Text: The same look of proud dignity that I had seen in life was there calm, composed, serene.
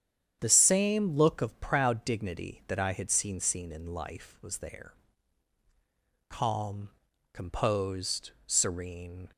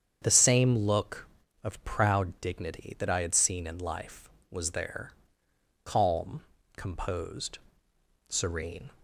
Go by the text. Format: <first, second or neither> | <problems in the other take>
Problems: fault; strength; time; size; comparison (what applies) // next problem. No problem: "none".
second | starts louder than the rest; strong; until 1.4 s; 8.5 dB; strong in the second // says "seen" twice; at 3.4 s // pauses between "there" and "calm"; strong; at 4.9 s; 1.3 s long; noticeable in the second